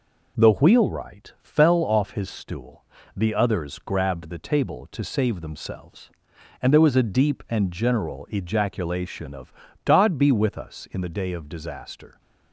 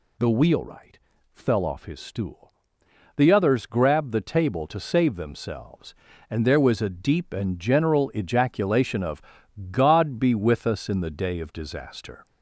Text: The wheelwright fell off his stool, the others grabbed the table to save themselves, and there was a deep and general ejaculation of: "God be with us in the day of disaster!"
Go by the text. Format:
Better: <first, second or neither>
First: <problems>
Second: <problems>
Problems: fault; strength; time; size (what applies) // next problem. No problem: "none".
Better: first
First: none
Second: gets louder; slight; throughout; 2.5 dB // pauses between "wheelwright" and "fell"; slight; at 0.9 s; 0.34 s long